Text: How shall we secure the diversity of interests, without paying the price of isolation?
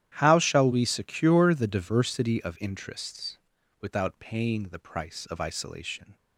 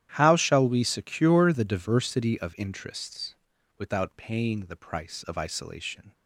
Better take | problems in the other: neither | starts louder than the rest; strong; the same in both

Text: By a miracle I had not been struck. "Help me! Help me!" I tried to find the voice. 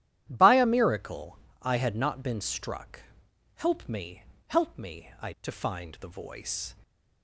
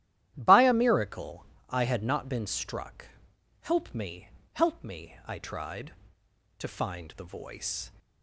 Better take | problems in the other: second | starts louder than the rest; strong; until 1.3 s; 12 dB; strong in the second // pauses between "miracle" and "I"; slight; at 1.3 s; 0.24 s long; slight in the second // skips "tried"; at 5.3 s

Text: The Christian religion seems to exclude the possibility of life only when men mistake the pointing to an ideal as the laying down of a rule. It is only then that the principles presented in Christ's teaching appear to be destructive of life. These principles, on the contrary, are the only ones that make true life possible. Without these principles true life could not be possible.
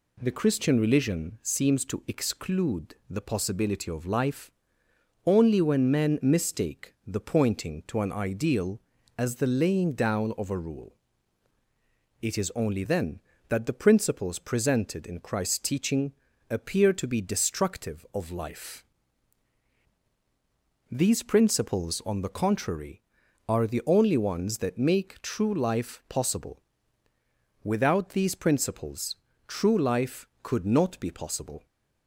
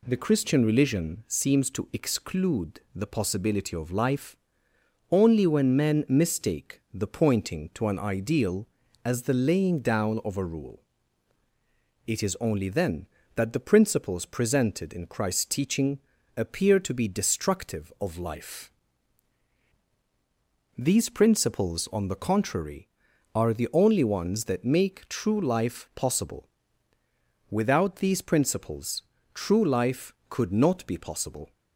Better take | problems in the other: neither | pauses between "life" and "only"; noticeable; the same in both // pauses between "teaching" and "appear"; slight; the same in both // pauses between "principles" and "true"; slight; the same in both

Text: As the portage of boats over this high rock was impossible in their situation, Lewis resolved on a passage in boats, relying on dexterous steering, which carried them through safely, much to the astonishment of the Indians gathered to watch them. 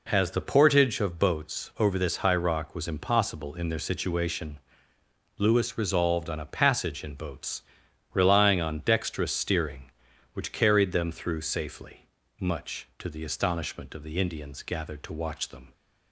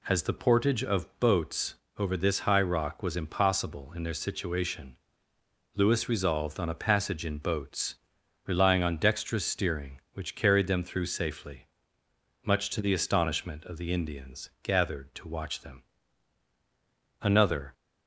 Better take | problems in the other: first | pauses between "boats" and "over"; slight; at 1.7 s; 0.22 s long // goes on to say "Another"; from 17.2 s on; 0.52 s long

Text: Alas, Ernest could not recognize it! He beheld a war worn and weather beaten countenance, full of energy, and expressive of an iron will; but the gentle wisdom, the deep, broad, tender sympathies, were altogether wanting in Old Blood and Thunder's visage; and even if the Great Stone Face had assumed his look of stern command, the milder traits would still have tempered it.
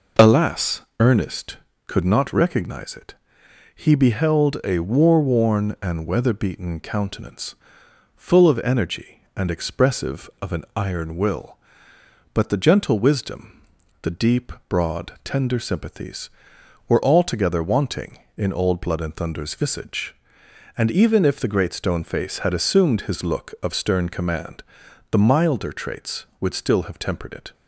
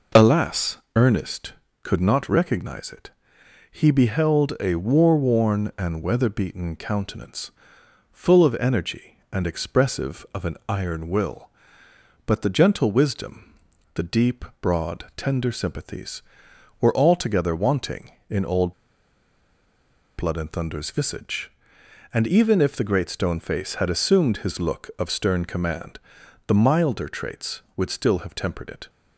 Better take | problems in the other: first | pauses between "Old" and "Blood"; strong; at 18.7 s; 1.4 s long

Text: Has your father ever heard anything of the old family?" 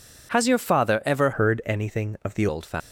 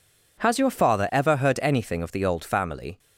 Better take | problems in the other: second | changes voice from "heard" to "the"; from 1.3 to 2.4 s; 1.1 s long

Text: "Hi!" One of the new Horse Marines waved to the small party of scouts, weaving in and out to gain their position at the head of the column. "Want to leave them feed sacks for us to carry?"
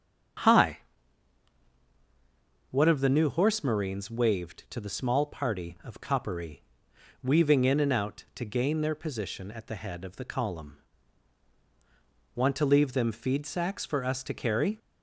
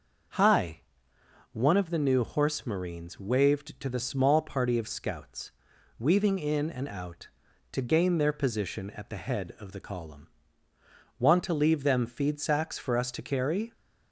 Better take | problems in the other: second | starts louder than the rest; strong; until 3.3 s; 7.5 dB // says "coppery" for "scouts"; at 5.9 s

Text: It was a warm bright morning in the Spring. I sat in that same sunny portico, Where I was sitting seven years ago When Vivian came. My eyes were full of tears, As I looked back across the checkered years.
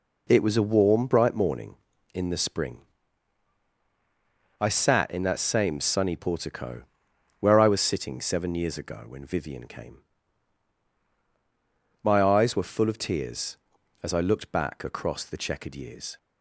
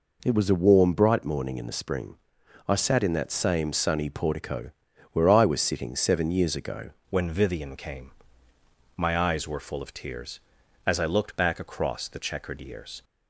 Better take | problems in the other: first | changes voice at "When"; from 7.0 s on; 6.0 s long

